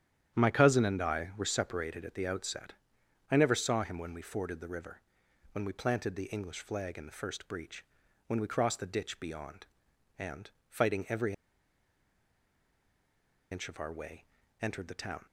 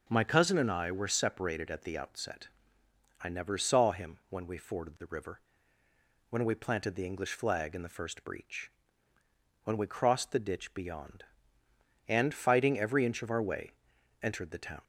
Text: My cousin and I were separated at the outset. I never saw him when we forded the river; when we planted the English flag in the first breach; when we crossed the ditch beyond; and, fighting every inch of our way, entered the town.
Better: second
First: starts louder than the rest; strong; until 1.4 s; 10 dB // pauses between "every" and "inch"; strong; at 11.3 s; 2.1 s long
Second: none

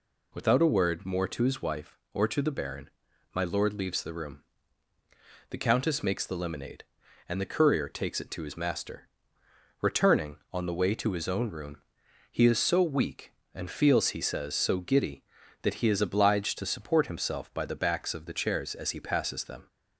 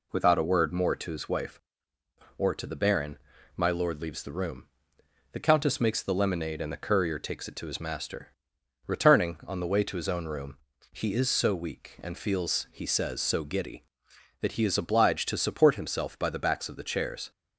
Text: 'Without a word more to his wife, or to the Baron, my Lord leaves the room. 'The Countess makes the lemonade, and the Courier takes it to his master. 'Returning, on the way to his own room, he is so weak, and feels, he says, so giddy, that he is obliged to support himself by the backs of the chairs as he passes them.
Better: first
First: none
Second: stops before "as he passes them"; at 17.3 s

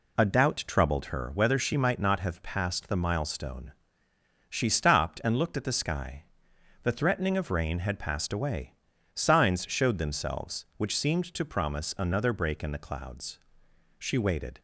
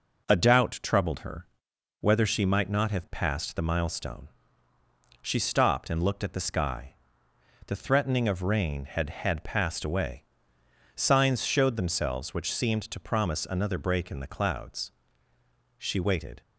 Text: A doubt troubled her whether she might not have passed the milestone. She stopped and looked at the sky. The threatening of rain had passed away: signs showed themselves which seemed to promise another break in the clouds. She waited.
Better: first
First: none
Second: pauses between "her" and "whether"; noticeable; at 1.4 s; 0.54 s long // says "had" twice; at 9.0 s

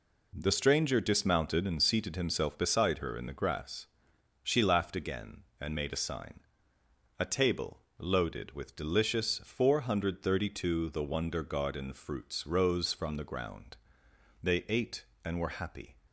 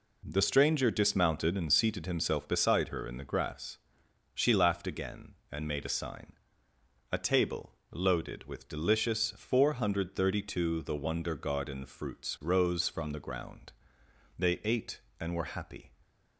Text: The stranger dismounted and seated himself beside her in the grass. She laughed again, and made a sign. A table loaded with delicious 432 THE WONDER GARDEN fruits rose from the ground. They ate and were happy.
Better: neither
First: pauses between "table" and "loaded"; slight; at 7.8 s; 0.16 s long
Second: pauses between "table" and "loaded"; slight; at 7.7 s; 0.16 s long

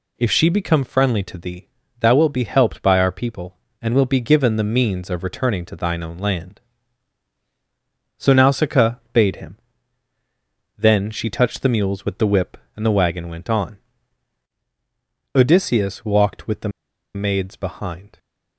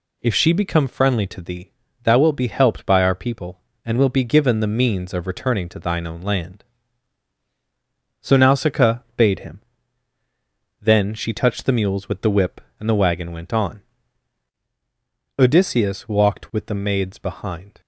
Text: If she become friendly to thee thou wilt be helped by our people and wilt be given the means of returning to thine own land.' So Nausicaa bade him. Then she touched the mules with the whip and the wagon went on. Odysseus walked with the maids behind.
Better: second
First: pauses between "thee" and "thou"; slight; at 1.6 s; 0.30 s long // pauses between "Nausicaa" and "bade"; slight; at 8.9 s; 0.16 s long // pauses between "the" and "maids"; noticeable; at 16.6 s; 0.46 s long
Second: pauses between "thee" and "thou"; slight; at 1.7 s; 0.30 s long // pauses between "Nausicaa" and "bade"; slight; at 8.9 s; 0.16 s long

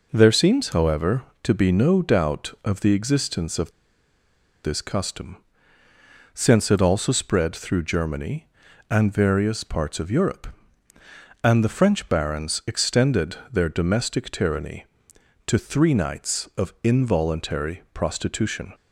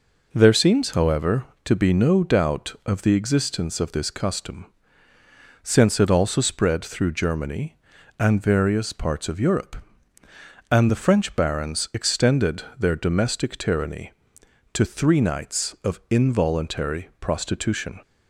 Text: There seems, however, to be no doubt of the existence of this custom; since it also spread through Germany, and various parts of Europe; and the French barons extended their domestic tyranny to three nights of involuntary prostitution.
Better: second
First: pauses between "of" and "this"; noticeable; at 3.6 s; 0.95 s long // pauses between "extended" and "their"; slight; at 13.3 s; 0.16 s long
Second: pauses between "extended" and "their"; slight; at 12.6 s; 0.16 s long

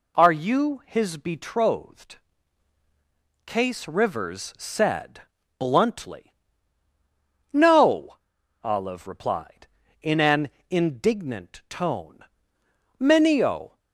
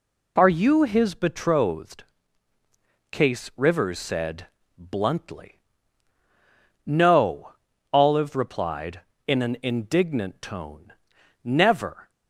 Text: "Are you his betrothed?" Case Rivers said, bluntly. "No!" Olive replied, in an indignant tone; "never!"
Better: second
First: pauses between "an" and "indignant"; slight; at 10.5 s; 0.18 s long // says "menio" for "never"; at 13.0 s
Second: none

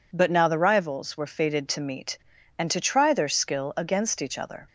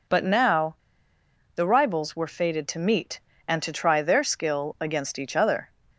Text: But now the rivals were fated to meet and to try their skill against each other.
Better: first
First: none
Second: pauses between "now" and "the"; noticeable; at 0.7 s; 0.79 s long

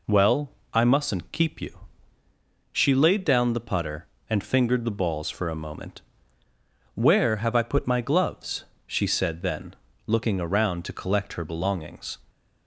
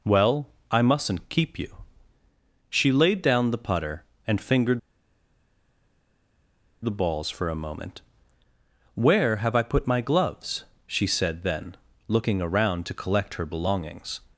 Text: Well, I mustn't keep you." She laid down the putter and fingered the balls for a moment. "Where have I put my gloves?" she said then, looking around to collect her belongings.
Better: first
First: none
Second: pauses between "fingered" and "the"; strong; at 4.7 s; 2.0 s long

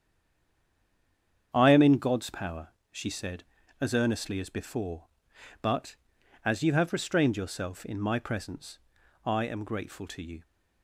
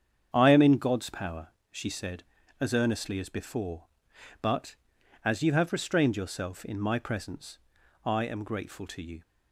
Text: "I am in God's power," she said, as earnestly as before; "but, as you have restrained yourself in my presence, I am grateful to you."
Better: second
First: stays silent before the first word; noticeable; until 1.5 s; 1.5 s long // starts louder than the rest; strong; until 2.5 s; 7.5 dB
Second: starts louder than the rest; strong; until 1.3 s; 7.5 dB

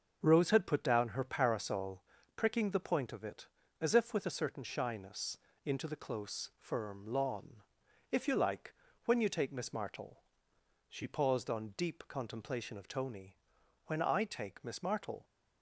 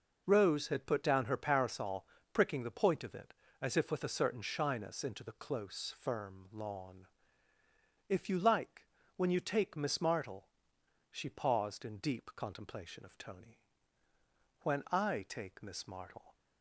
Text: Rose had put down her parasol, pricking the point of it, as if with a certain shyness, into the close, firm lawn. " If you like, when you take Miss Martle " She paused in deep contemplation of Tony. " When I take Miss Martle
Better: second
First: starts louder than the rest; until 1.2 s; 6.5 dB // says "on" for "in"; at 11.4 s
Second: none

